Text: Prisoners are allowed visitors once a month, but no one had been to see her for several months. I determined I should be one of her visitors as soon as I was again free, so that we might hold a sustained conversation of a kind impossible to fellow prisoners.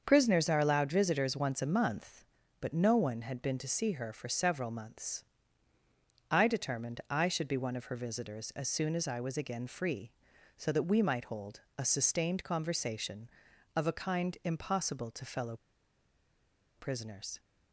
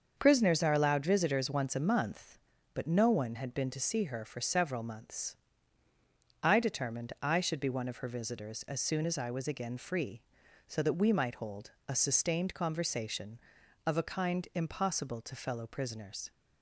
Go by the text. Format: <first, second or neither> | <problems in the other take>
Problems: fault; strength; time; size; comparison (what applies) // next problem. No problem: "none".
second | starts louder than the rest; until 1.0 s; 6.5 dB; also in the second // pauses between "hold" and "a"; slight; at 11.6 s; 0.18 s long; slight in the second // pauses between "fellow" and "prisoners"; at 15.5 s; 1.2 s long